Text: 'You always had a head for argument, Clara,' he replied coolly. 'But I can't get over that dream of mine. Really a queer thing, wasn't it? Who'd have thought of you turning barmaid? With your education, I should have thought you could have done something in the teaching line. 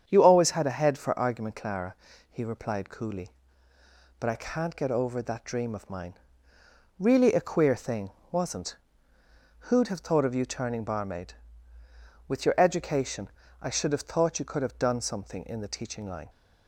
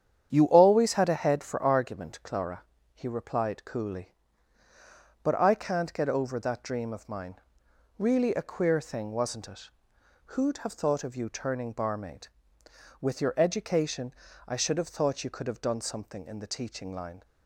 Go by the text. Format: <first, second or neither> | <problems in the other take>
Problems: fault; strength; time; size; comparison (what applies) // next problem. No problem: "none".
second | starts louder than the rest; strong; until 1.1 s; 8 dB; strong in the second // skips "it"; at 9.1 s